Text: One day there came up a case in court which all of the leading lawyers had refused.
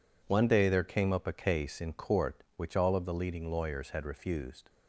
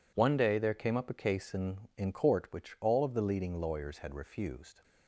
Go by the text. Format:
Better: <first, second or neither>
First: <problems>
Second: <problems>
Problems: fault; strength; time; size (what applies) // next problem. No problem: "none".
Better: first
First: none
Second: says "in" twice; at 1.9 s